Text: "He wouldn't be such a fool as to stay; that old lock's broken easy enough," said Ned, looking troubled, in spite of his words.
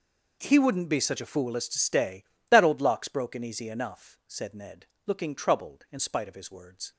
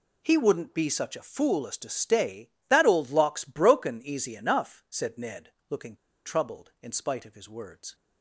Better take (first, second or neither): first